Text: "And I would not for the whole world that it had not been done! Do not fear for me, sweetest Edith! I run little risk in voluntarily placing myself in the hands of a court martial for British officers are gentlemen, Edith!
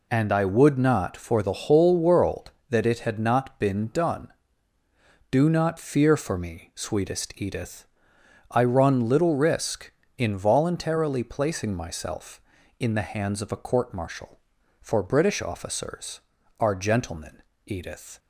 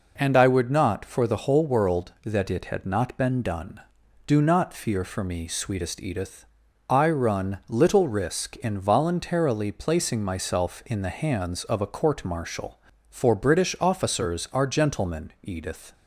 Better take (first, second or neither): neither